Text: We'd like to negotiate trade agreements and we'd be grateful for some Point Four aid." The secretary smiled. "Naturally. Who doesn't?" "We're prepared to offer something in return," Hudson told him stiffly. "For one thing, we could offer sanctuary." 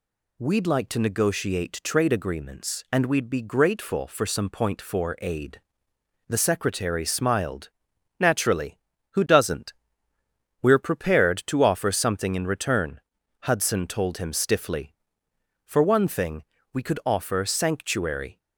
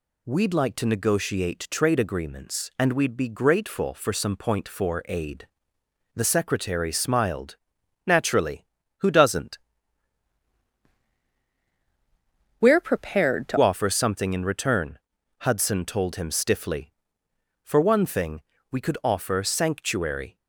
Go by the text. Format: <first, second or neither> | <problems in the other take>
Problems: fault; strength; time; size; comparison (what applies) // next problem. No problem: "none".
first | changes voice from "We're" to "to"; from 12.5 to 13.5 s; 1.0 s long